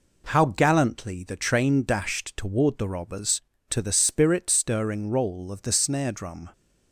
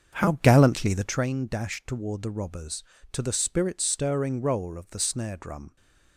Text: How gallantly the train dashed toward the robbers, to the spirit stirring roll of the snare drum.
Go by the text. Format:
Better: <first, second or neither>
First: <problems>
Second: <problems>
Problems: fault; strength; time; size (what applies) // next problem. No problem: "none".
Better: first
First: none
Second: starts louder than the rest; until 1.2 s; 7 dB